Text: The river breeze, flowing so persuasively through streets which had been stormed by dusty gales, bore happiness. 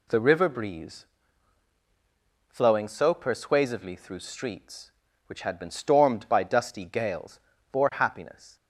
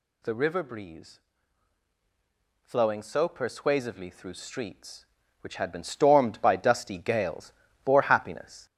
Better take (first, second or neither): first